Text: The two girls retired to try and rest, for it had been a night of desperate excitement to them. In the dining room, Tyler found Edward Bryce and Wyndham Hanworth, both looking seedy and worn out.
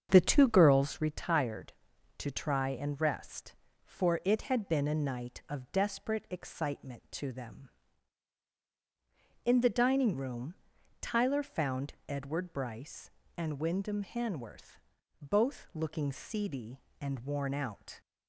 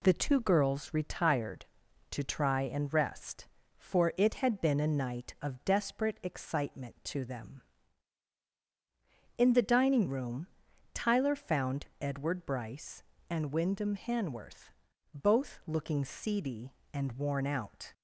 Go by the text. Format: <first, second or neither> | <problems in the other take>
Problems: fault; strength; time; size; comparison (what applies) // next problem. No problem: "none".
second | starts louder than the rest; until 1.1 s; 7 dB // pauses between "found" and "Edward"; slight; at 11.9 s; 0.16 s long; slight in the second